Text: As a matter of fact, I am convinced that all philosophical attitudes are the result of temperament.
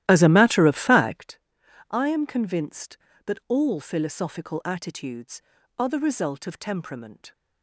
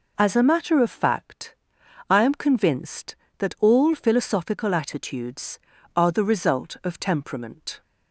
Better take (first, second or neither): second